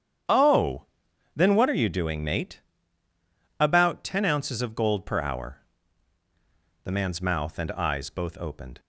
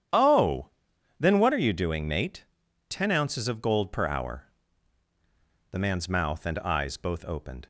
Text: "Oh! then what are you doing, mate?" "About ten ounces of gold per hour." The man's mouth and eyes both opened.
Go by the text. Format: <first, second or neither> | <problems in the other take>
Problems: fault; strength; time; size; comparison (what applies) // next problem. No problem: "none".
first | starts louder than the rest; strong; until 1.6 s; 9.5 dB; strong in the first // skips "About"; at 2.6 s